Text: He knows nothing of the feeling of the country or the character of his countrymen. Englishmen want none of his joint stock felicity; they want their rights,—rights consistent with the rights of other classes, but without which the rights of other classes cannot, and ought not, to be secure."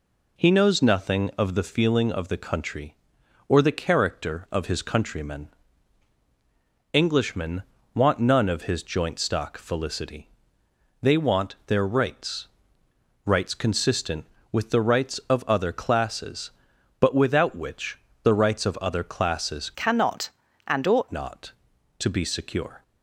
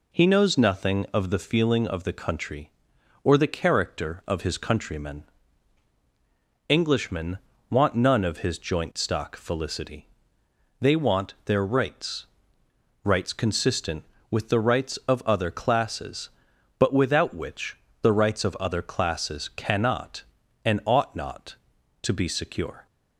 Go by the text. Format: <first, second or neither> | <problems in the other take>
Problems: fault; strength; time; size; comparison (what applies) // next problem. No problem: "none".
second | pauses between "Englishmen" and "want"; slight; at 7.6 s; 0.32 s long; slight in the second // pauses between "which" and "the"; slight; at 17.9 s; 0.24 s long; slight in the second // changes voice from "cannot" to "ought"; from 19.7 to 21.0 s; 1.3 s long